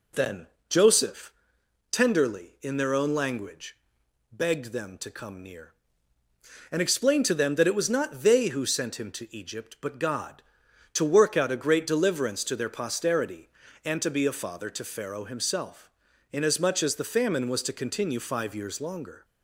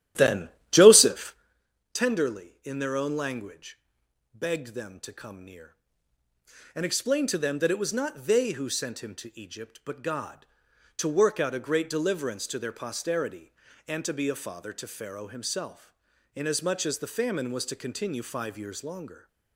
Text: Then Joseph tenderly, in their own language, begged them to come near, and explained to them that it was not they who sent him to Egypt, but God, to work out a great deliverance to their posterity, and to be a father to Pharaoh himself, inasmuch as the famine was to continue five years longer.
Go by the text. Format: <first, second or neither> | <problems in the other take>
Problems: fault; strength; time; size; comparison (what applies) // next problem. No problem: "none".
first | starts louder than the rest; strong; until 1.6 s; 13 dB // pauses between "Then" and "Joseph"; slight; at 0.4 s; 0.22 s long; slight in the first // pauses between "Joseph" and "tenderly"; noticeable; at 1.3 s; 0.58 s long; noticeable in the first